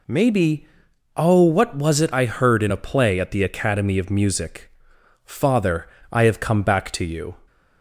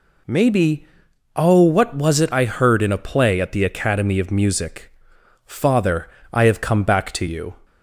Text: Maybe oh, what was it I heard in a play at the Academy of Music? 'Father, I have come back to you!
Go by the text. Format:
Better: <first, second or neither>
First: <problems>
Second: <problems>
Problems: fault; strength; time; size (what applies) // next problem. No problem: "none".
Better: neither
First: pauses between "Maybe" and "oh"; noticeable; at 0.6 s; 0.48 s long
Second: pauses between "Maybe" and "oh"; noticeable; at 0.8 s; 0.48 s long